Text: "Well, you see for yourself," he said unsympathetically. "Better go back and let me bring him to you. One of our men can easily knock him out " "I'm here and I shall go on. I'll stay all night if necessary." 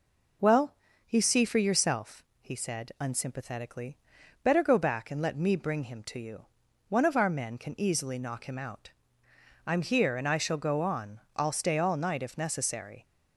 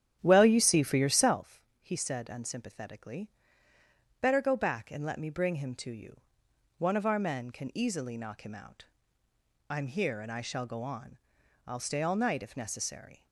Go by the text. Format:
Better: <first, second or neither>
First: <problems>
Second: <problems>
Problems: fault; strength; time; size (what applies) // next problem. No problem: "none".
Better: first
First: none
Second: starts louder than the rest; strong; until 1.4 s; 10 dB